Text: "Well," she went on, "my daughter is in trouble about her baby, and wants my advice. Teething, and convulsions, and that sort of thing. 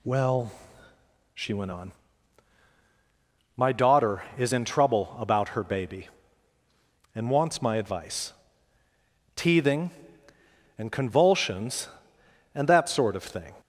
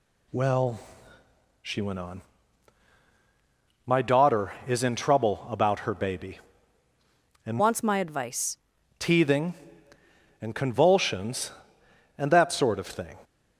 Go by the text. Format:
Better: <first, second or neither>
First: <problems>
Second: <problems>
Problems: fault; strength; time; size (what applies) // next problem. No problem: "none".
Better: first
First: none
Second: changes voice from "wants" to "advice"; from 7.5 to 8.5 s; 1.0 s long